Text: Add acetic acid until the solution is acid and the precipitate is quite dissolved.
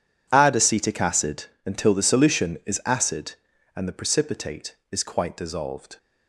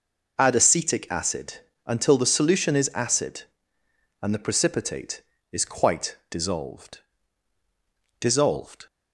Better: first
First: pauses between "acid" and "until"; slight; at 1.4 s; 0.18 s long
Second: pauses between "acid" and "until"; slight; at 1.5 s; 0.30 s long // says "dissolved" twice; at 8.1 s

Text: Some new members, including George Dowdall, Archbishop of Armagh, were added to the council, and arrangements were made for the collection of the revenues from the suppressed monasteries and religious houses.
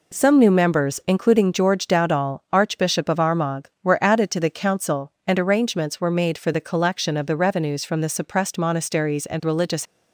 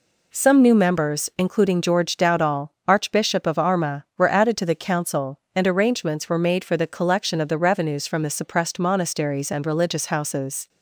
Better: second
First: stops before "houses"; at 9.8 s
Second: none

